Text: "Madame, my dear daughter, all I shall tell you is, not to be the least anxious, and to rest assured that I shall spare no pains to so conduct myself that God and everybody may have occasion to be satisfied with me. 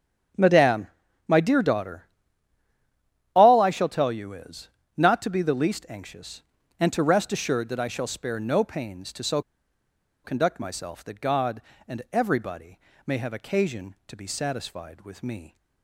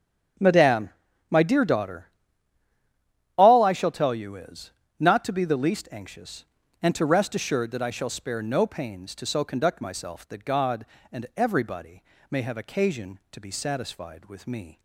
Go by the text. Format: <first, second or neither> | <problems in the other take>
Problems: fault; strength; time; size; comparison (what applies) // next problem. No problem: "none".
second | starts louder than the rest; strong; until 1.7 s; 8 dB; strong in the second // pauses between "so" and "conduct"; noticeable; at 9.4 s; 0.83 s long // pauses between "everybody" and "may"; slight; at 12.7 s; 0.28 s long; slight in the second